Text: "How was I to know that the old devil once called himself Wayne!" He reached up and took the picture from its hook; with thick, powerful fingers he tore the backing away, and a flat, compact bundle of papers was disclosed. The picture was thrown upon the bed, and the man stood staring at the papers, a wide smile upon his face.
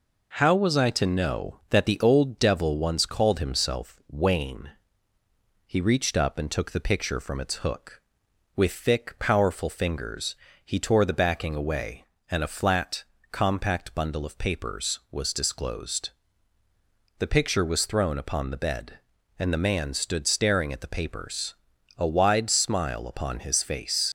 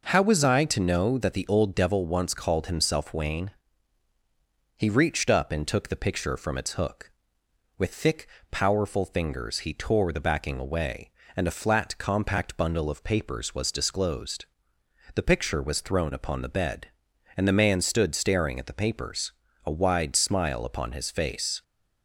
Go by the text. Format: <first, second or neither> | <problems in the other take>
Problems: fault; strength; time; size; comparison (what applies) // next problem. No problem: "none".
second | pauses between "fingers" and "he"; slight; at 10.3 s; 0.26 s long // leaves "face" unfinished; at 24.0 s; 85 ms